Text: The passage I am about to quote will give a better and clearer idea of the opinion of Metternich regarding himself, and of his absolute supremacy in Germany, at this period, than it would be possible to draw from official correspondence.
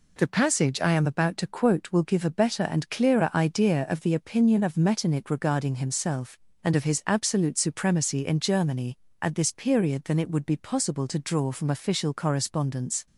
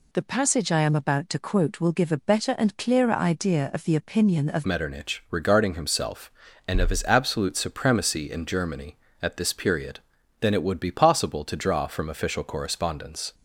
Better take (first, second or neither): first